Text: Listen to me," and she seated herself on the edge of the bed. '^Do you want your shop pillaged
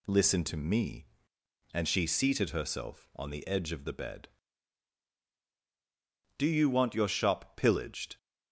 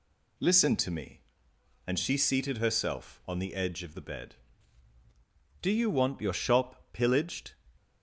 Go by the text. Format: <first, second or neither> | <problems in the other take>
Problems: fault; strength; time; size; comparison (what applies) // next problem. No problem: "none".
neither | none